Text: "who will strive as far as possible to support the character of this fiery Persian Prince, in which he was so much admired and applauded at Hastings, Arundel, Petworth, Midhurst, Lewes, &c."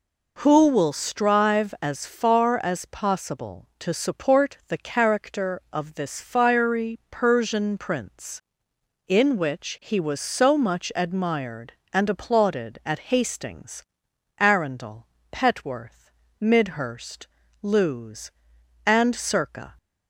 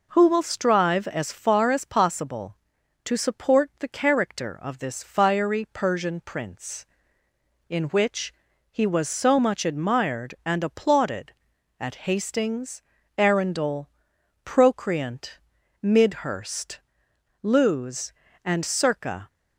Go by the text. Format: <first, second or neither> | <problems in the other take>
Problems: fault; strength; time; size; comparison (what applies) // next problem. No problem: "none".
first | pauses between "which" and "he"; at 8.3 s; 0.38 s long // says "Procreant" for "Petworth"; at 14.4 s